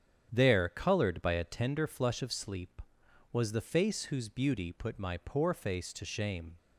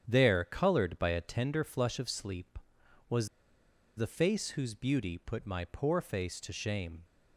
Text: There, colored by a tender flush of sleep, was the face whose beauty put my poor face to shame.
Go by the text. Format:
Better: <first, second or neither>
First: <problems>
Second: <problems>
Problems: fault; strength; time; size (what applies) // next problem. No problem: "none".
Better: first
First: starts louder than the rest; strong; until 1.3 s; 9 dB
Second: starts louder than the rest; strong; until 1.0 s; 9 dB // pauses between "was" and "the"; noticeable; at 3.2 s; 0.70 s long